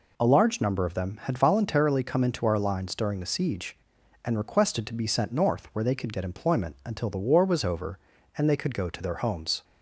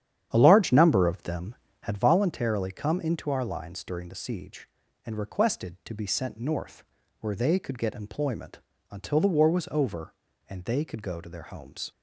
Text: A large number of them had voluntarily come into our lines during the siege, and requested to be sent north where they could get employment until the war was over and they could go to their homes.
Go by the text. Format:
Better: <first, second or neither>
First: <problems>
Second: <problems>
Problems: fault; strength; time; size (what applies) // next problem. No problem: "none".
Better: first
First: none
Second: starts louder than the rest; strong; until 2.1 s; 10 dB // pauses between "north" and "where"; slight; at 6.8 s; 0.34 s long // pauses between "employment" and "until"; slight; at 8.5 s; 0.32 s long